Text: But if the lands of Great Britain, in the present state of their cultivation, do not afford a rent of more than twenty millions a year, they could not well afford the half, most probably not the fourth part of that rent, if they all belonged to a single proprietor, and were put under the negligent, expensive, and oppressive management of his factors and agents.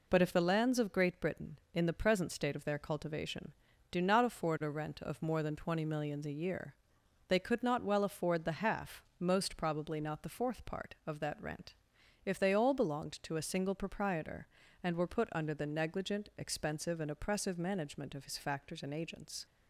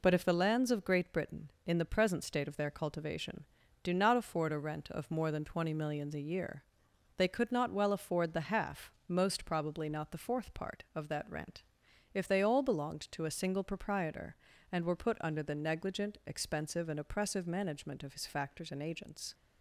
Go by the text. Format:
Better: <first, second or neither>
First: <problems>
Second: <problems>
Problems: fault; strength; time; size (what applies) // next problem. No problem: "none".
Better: neither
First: none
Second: none